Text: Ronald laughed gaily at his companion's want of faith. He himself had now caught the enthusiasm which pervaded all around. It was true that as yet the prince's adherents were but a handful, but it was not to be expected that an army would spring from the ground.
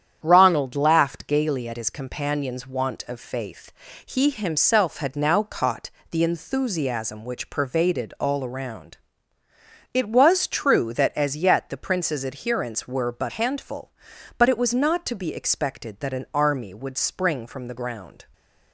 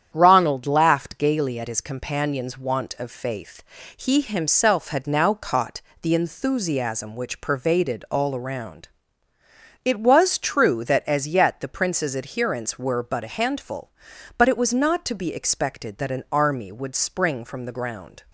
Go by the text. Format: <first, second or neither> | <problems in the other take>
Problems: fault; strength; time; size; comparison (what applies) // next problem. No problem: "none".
second | starts louder than the rest; strong; until 1.2 s; 9 dB; strong in the second // pauses between "caught" and "the"; slight; at 5.8 s; 0.22 s long; slight in the second // skips "a"; at 13.2 s // stays silent after the last word; slight; from 18.2 s on; 0.5 s long